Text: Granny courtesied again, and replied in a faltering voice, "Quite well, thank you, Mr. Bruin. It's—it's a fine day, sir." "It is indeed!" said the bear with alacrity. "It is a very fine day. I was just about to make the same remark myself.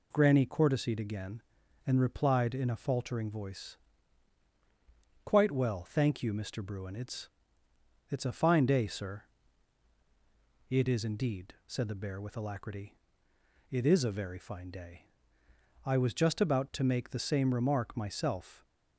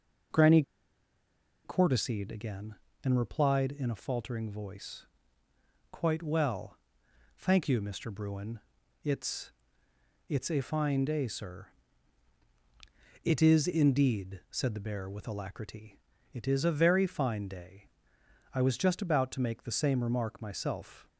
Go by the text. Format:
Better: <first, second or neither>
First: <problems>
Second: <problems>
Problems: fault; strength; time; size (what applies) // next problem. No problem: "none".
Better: first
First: none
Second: pauses between "Granny" and "courtesied"; at 0.6 s; 1.0 s long